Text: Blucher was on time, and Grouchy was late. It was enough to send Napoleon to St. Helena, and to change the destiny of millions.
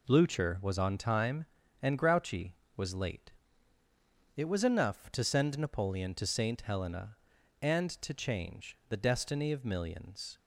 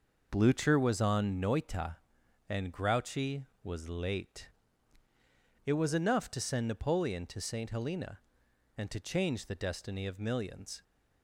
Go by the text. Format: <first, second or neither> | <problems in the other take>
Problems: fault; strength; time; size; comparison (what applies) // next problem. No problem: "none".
first | says "noita" for "time"; at 1.4 s